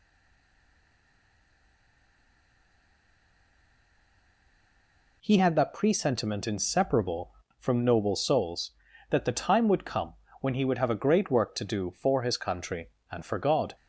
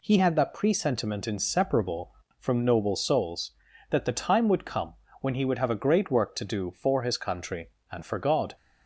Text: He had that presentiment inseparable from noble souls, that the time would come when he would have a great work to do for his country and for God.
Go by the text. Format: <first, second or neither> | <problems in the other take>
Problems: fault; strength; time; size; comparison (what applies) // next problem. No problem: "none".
second | stays silent before the first word; strong; until 5.2 s; 5.2 s long // pauses between "come" and "when"; slight; at 10.1 s; 0.26 s long; slight in the second